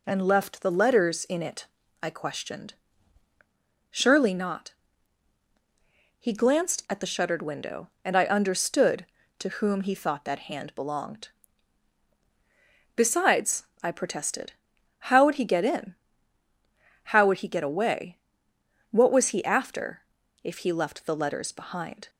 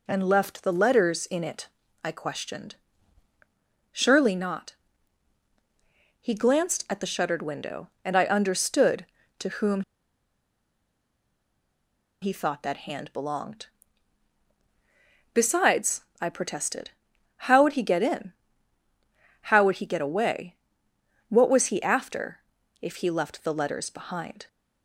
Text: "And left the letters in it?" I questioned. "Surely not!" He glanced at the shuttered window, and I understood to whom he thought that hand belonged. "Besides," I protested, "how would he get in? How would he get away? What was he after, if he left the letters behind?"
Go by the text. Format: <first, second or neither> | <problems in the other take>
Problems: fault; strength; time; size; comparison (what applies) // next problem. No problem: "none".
first | pauses between "whom" and "he"; strong; at 9.8 s; 2.4 s long